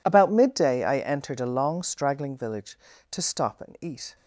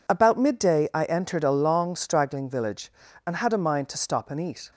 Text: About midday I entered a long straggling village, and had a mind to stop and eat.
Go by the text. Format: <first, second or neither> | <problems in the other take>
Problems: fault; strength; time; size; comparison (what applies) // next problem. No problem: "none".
second | skips "and had a mind"; at 2.9 s